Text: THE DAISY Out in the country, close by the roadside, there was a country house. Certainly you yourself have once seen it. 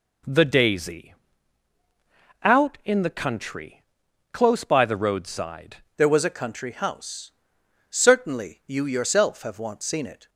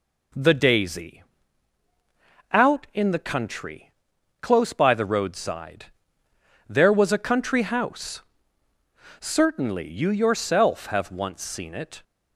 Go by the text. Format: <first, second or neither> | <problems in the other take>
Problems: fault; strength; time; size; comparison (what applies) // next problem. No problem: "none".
second | pauses between "DAISY" and "Out"; strong; at 1.1 s; 1.3 s long; strong in the second // changes voice at "there"; from 5.9 s on; 4.3 s long